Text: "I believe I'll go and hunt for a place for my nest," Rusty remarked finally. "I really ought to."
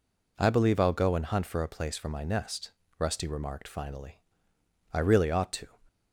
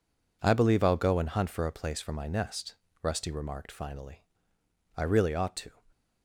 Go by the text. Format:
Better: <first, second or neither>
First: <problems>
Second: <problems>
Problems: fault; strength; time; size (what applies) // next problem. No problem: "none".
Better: first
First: none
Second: gets quieter; strong; throughout; 9 dB